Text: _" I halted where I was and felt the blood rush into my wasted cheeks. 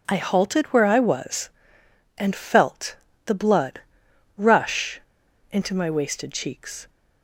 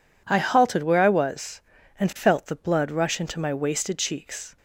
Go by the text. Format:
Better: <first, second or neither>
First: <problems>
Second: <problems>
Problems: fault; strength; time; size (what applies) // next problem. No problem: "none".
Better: second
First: pauses between "felt" and "the"; slight; at 2.9 s; 0.30 s long // pauses between "blood" and "rush"; noticeable; at 3.8 s; 0.58 s long // pauses between "rush" and "into"; noticeable; at 5.0 s; 0.52 s long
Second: none